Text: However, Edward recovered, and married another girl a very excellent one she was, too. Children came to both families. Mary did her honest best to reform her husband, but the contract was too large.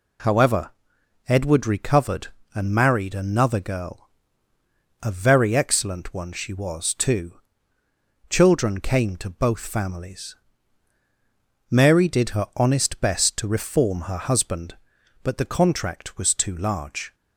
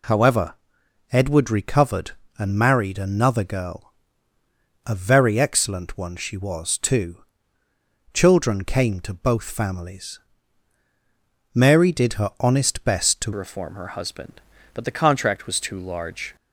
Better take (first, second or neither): first